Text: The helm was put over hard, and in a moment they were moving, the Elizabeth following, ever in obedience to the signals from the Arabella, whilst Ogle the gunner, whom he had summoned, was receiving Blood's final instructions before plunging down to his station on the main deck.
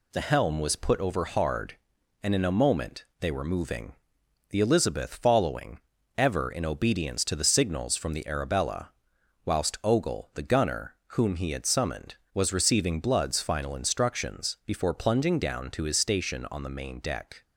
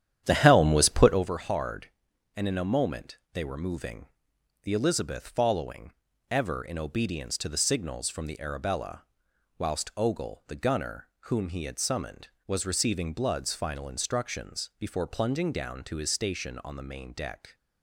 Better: first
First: pauses between "moment" and "they"; slight; at 3.0 s; 0.16 s long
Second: starts louder than the rest; strong; until 1.3 s; 10 dB // pauses between "moment" and "they"; slight; at 3.1 s; 0.16 s long

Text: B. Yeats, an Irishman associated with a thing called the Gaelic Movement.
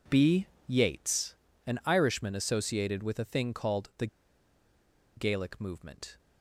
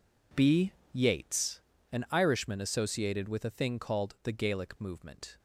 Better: second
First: pauses between "the" and "Gaelic"; at 4.0 s; 1.1 s long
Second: none

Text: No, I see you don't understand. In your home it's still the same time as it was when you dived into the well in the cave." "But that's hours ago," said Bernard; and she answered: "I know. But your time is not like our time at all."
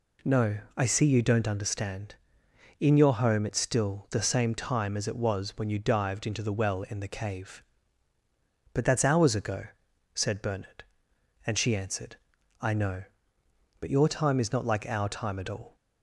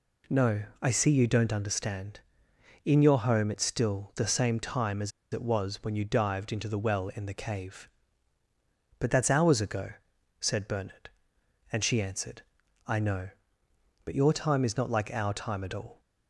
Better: first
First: none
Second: pauses between "as" and "it"; slight; at 5.1 s; 0.23 s long

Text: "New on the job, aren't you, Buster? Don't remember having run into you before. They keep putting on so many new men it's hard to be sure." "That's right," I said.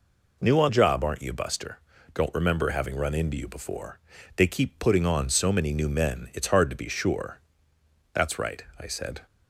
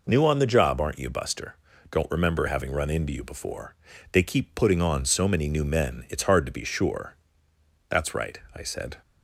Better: second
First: skips "the"; at 0.6 s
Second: none

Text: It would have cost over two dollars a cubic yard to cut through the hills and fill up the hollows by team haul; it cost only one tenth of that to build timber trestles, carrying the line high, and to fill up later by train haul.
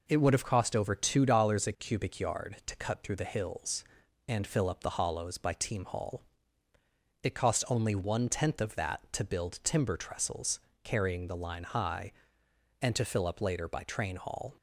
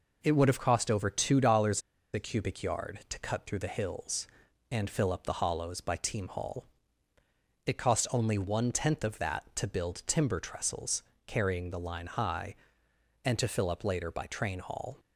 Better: first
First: none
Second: pauses between "dollars" and "a"; slight; at 1.8 s; 0.32 s long

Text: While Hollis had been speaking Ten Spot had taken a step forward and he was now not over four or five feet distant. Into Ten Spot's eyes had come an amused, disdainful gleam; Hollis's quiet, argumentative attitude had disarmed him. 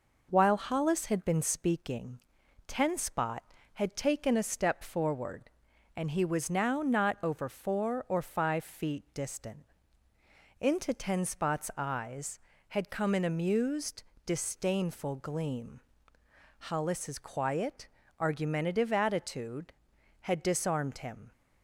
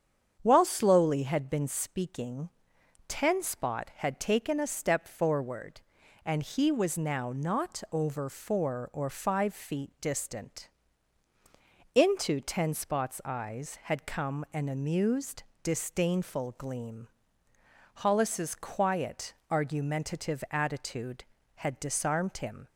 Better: first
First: pauses between "speaking" and "Ten"; noticeable; at 2.1 s; 0.48 s long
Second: starts louder than the rest; strong; until 1.4 s; 8 dB // says "Slowly" for "Hollis"; at 0.6 s // pauses between "speaking" and "Ten"; noticeable; at 2.4 s; 0.58 s long

